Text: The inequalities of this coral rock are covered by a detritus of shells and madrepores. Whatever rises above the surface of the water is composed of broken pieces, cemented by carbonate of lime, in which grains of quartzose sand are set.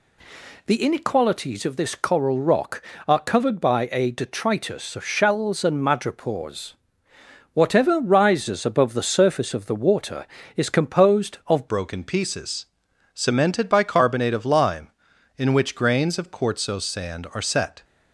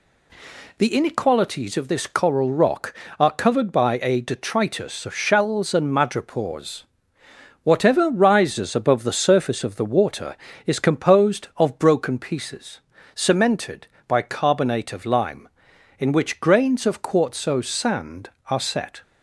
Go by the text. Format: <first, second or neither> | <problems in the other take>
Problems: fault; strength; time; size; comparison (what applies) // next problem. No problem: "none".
second | changes voice at "broken"; from 11.6 s on; 6.2 s long